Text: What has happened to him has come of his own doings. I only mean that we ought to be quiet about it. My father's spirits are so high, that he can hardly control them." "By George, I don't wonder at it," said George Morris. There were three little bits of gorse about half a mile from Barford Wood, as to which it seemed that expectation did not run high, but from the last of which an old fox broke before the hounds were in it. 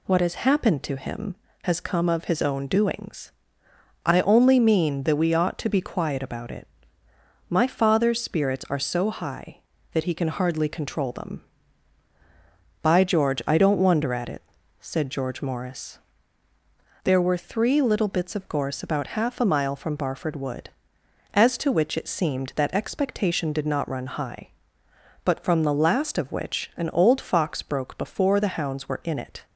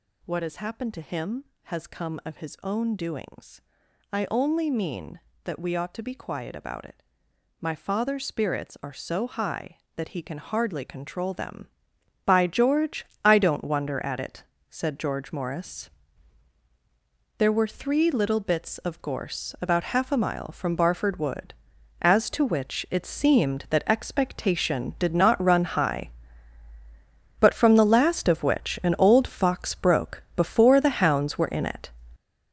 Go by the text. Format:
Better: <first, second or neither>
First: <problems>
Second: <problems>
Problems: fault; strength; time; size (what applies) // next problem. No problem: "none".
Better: first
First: none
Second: gets louder; strong; throughout; 9 dB